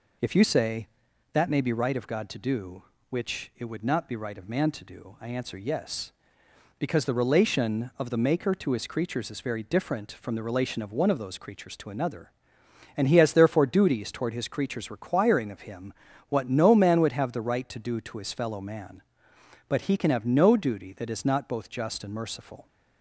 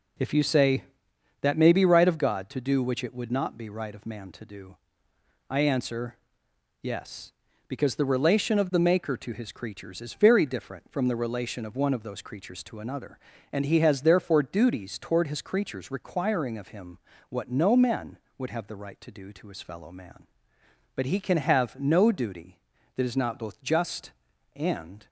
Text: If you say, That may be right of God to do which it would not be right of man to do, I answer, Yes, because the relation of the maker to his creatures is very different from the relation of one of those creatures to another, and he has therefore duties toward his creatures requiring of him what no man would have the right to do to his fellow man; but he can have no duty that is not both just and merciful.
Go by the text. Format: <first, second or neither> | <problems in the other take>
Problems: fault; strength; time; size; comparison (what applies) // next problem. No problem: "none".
first | pauses between "him" and "what"; slight; at 16.9 s; 0.32 s long; slight in the first // stops before "merciful"; at 25.0 s